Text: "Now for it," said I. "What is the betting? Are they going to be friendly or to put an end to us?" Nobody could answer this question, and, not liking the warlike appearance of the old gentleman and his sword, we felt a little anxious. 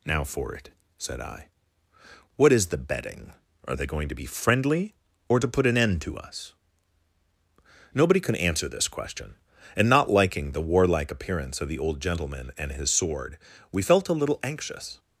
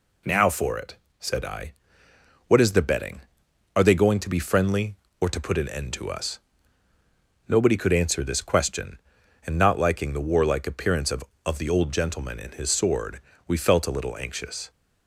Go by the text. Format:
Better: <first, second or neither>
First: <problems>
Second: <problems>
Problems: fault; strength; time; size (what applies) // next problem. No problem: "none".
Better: first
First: none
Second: says "of" twice; at 11.4 s